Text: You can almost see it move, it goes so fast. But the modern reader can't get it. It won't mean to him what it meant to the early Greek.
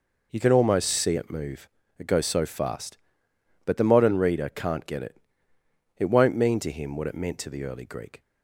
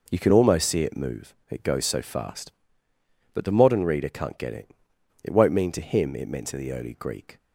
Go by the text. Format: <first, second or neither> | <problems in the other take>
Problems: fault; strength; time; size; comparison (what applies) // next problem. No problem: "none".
first | skips "what"; at 6.1 s